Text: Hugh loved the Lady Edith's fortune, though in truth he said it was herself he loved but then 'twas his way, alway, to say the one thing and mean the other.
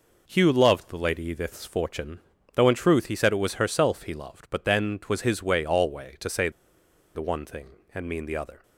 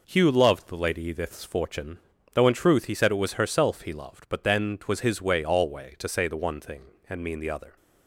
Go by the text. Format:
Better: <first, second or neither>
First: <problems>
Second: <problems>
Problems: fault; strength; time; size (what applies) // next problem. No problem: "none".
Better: second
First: pauses between "say" and "the"; noticeable; at 6.4 s; 0.65 s long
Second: none